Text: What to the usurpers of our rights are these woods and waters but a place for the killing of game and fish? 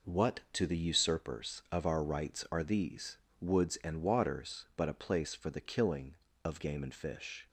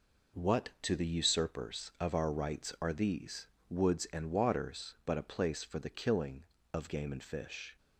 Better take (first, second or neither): neither